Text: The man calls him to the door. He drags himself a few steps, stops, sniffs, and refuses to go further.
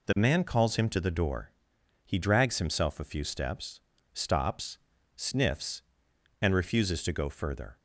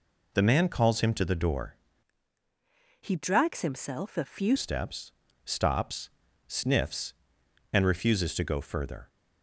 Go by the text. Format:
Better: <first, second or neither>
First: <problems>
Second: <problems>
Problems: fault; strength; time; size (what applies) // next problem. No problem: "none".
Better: first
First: none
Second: changes voice from "He" to "few"; from 3.0 to 4.5 s; 1.5 s long